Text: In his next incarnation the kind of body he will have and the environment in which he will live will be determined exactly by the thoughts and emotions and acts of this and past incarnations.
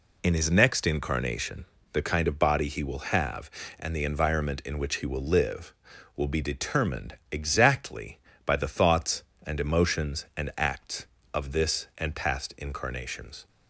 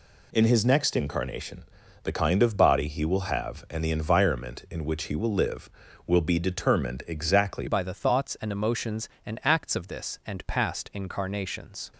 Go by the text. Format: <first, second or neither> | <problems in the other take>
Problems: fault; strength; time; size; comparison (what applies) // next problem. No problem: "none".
first | pauses between "incarnation" and "the"; at 1.6 s; 0.38 s long; slight in the first // changes voice at "by"; from 7.6 s on; 4.3 s long